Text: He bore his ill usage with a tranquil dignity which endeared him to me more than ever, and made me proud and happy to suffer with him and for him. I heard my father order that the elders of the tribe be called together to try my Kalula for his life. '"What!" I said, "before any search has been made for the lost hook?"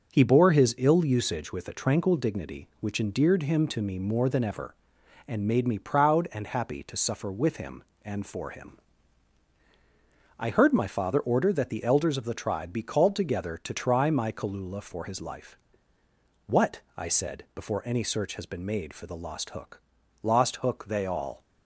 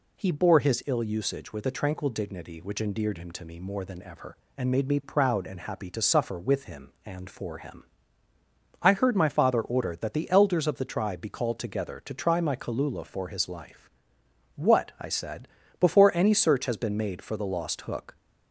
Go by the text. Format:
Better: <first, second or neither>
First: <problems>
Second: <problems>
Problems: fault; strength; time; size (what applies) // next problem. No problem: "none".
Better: second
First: goes on to say "Lost hook they all"; noticeable; from 20.2 s on; 1.2 s long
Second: none